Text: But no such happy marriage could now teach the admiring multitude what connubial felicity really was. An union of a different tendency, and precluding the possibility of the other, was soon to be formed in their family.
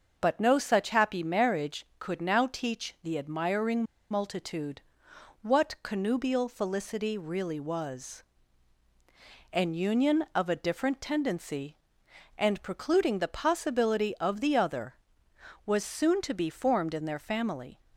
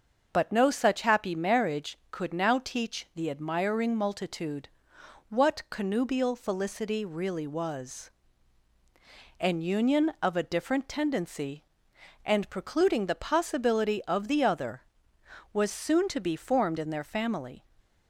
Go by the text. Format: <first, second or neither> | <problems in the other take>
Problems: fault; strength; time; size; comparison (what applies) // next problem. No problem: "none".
second | starts louder than the rest; until 1.1 s; 6 dB; also in the second // pauses between "admiring" and "multitude"; slight; at 3.8 s; 0.27 s long // pauses between "multitude" and "what"; noticeable; at 4.8 s; 0.60 s long; noticeable in the second